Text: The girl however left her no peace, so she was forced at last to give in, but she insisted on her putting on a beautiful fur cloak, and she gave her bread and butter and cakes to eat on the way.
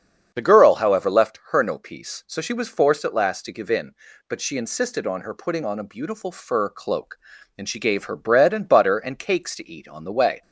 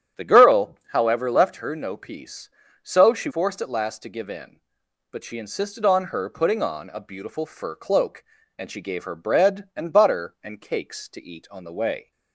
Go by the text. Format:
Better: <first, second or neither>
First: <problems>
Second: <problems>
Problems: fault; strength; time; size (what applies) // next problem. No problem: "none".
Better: first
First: starts louder than the rest; strong; until 1.3 s; 7.5 dB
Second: starts louder than the rest; strong; until 1.3 s; 9 dB // skips "was"; at 3.3 s